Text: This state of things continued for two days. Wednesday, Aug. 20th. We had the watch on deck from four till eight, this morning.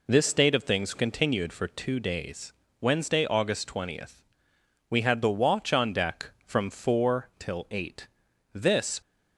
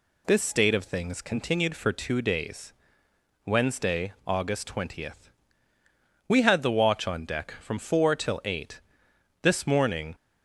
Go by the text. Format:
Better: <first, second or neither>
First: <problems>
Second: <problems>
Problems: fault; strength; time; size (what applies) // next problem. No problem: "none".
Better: second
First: stops before "morning"; at 9.0 s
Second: none